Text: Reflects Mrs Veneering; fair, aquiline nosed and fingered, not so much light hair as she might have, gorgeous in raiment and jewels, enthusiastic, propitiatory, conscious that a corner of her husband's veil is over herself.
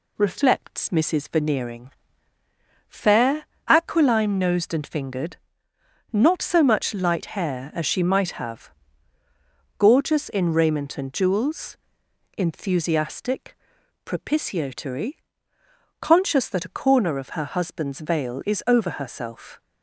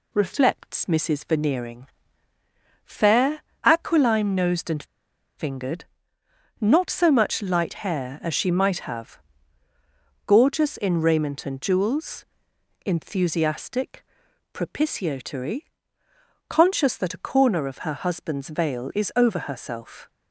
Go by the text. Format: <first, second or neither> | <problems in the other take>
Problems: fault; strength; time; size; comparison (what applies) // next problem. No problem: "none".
first | pauses between "and" and "fingered"; noticeable; at 4.8 s; 0.53 s long